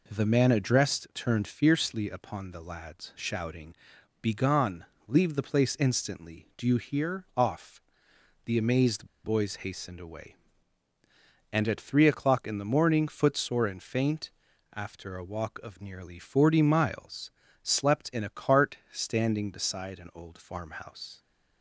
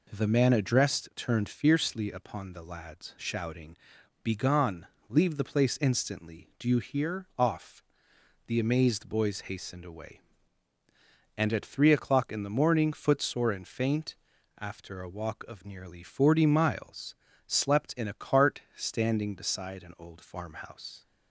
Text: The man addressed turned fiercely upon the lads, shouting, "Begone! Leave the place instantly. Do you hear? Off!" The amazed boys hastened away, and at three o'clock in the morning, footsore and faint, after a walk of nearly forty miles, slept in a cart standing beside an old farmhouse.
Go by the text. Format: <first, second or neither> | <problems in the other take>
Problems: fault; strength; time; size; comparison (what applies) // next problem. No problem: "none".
second | pauses between "amazed" and "boys"; slight; at 9.0 s; 0.18 s long // pauses between "cart" and "standing"; slight; at 18.7 s; 0.16 s long; slight in the second